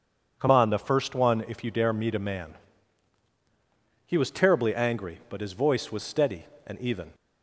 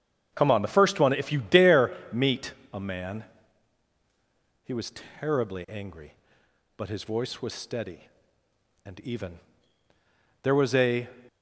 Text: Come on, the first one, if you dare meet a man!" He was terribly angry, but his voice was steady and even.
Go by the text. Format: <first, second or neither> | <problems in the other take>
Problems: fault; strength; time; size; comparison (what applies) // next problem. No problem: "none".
first | starts louder than the rest; strong; until 1.3 s; 8 dB // pauses between "dare" and "meet"; slight; at 1.9 s; 0.20 s long // pauses between "meet" and "a"; slight; at 2.5 s; 0.18 s long // pauses between "was" and "terribly"; slight; at 4.9 s; 0.28 s long // goes on to say "There was a"; noticeable; from 10.4 s on; 0.66 s long